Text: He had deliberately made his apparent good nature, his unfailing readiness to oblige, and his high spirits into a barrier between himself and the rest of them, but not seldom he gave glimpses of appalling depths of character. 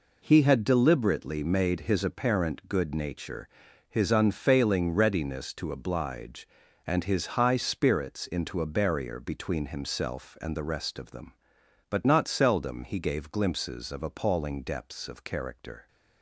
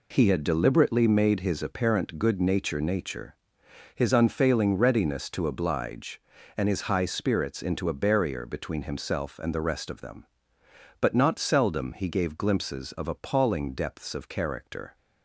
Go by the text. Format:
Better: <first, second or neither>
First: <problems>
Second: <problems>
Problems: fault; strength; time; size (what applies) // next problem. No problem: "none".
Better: first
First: none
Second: says "nature" twice; at 2.8 s